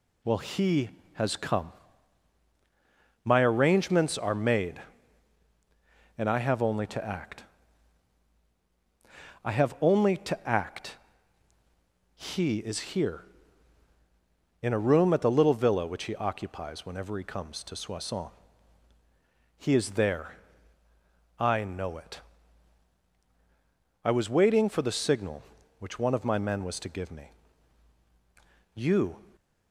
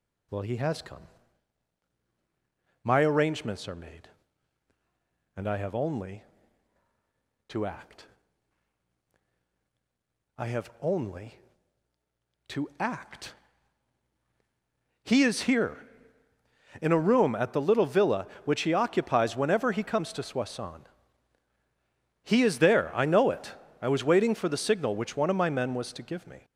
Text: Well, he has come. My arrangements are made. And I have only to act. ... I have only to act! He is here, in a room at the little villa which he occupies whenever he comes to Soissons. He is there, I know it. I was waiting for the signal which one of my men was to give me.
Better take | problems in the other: second | goes on to say "You"; slight; from 28.7 s on; 0.46 s long

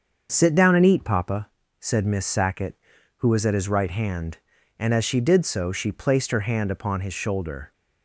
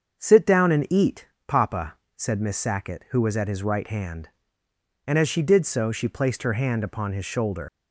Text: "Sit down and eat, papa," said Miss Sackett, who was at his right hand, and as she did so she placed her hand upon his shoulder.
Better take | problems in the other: first | starts louder than the rest; until 1.2 s; 7 dB; also in the first // leaves "shoulder" unfinished; at 7.6 s; 115 ms

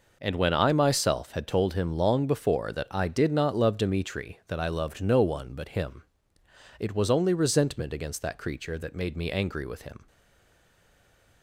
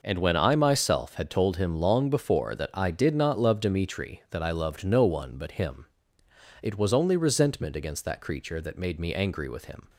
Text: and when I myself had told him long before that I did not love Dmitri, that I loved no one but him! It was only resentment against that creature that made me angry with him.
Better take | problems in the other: second | stays silent after the last word; noticeable; from 10.0 s on; 1.4 s long

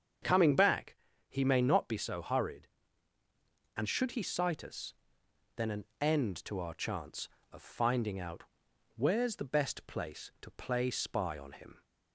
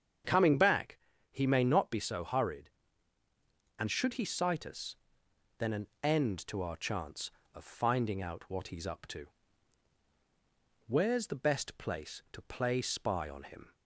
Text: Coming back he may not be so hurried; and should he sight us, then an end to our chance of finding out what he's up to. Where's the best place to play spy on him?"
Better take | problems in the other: second | starts louder than the rest; strong; until 1.5 s; 7.5 dB; strong in the second // pauses between "back" and "he"; slight; at 0.9 s; 0.34 s long; slight in the second // pauses between "an" and "end"; slight; at 5.8 s; 0.16 s long; slight in the second // skips "what he's up to"; at 8.7 s

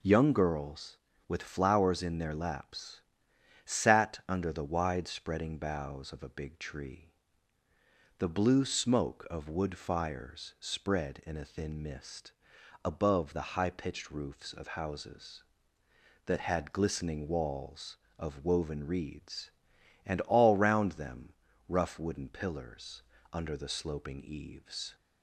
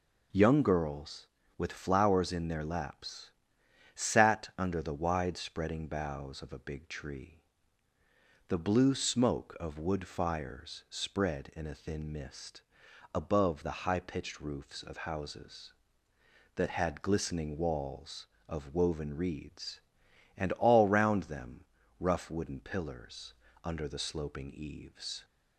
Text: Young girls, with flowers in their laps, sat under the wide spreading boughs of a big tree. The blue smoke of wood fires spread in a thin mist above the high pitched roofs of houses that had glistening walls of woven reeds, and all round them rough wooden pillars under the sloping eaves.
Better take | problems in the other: neither | pauses between "mist" and "above"; noticeable; the same in both // pauses between "them" and "rough"; slight; the same in both // pauses between "pillars" and "under"; slight; the same in both

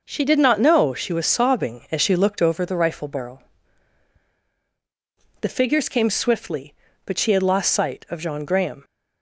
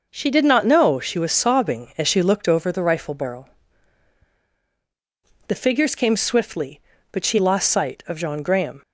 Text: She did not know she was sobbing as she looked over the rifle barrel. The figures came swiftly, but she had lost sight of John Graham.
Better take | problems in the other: first | skips "had"; at 7.3 s

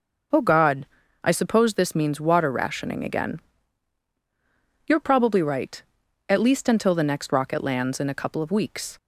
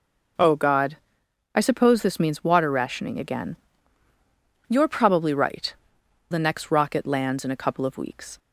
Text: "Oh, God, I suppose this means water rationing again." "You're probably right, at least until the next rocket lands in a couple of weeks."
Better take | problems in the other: first | skips "at least until"; at 6.0 s

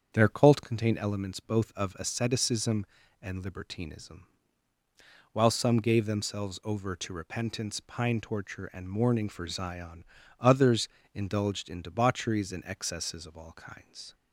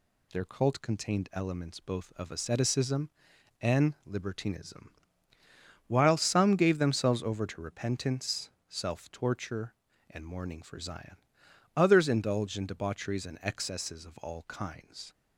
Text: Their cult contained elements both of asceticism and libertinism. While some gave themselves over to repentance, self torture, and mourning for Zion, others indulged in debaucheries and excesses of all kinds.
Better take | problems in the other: second | starts louder than the rest; strong; until 1.1 s; 7.5 dB // says "pine" for "self"; at 7.8 s // pauses between "others" and "indulged"; slight; at 10.8 s; 0.26 s long

